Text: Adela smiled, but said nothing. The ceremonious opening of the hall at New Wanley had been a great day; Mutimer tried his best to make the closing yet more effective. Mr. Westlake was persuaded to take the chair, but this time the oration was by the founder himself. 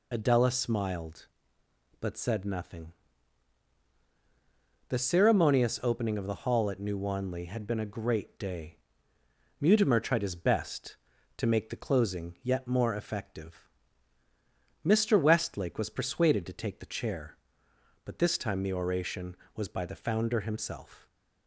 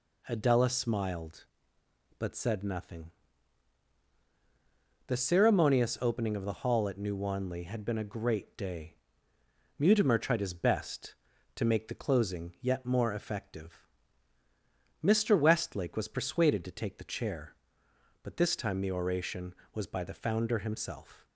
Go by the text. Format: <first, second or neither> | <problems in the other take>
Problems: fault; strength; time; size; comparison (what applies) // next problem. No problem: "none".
second | loses the start of "Adela"; at 0.1 s; 55 ms